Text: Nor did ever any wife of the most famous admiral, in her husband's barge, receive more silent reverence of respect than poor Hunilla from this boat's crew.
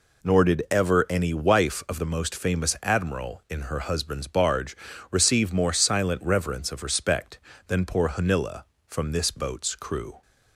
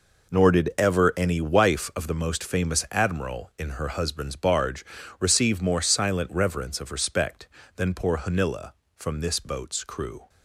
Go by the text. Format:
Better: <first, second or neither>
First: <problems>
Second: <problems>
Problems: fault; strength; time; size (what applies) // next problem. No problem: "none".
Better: first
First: none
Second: gets quieter; strong; throughout; 11.5 dB